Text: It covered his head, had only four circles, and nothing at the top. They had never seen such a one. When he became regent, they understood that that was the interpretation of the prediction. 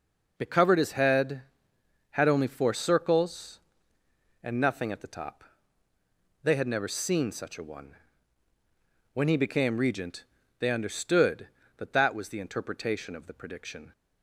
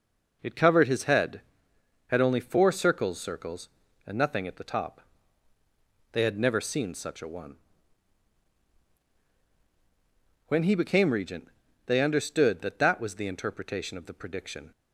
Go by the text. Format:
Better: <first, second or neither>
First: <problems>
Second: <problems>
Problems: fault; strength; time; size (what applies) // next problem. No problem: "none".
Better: first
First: none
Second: says "circles" twice; at 3.1 s